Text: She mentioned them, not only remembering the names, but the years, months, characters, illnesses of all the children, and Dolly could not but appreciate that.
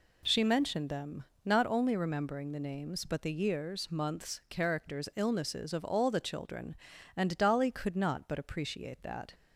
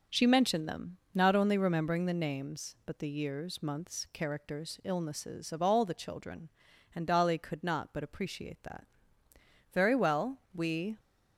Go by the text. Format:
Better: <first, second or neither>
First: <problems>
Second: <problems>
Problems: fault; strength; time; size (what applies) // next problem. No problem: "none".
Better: first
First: none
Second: goes on to say "Very well we"; noticeable; from 9.7 s on; 1.2 s long